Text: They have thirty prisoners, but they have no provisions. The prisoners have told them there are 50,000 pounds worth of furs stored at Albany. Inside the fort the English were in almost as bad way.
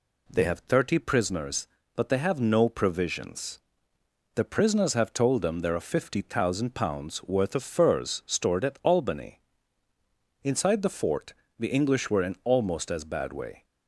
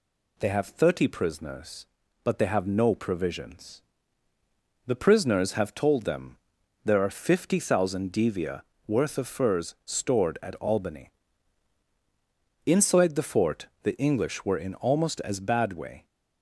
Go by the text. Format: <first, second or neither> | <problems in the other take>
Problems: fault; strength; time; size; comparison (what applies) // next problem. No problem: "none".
first | pauses between "them" and "there"; noticeable; at 6.3 s; 0.46 s long // says "devia" for "pounds"; at 8.1 s // pauses between "fort" and "the"; slight; at 13.6 s; 0.16 s long; slight in the first